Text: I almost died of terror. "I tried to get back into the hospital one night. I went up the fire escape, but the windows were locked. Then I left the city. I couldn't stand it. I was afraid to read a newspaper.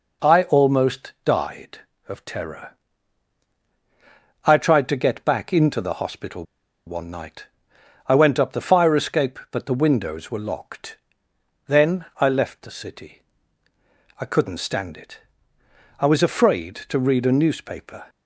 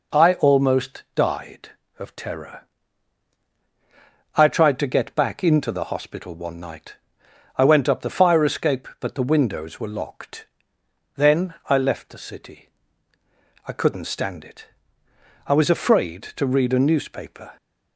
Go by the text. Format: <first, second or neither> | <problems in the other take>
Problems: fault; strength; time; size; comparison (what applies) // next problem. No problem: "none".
second | pauses between "hospital" and "one"; at 6.4 s; 0.42 s long